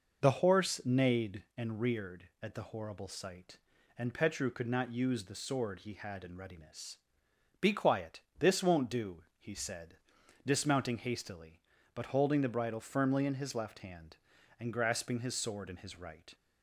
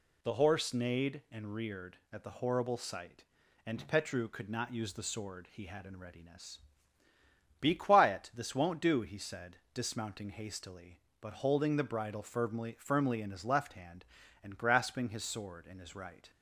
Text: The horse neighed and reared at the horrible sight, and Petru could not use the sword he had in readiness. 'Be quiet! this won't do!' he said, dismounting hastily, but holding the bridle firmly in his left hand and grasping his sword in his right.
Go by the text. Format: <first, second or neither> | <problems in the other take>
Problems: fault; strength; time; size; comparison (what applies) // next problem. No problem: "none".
first | says "firmly" twice; at 12.7 s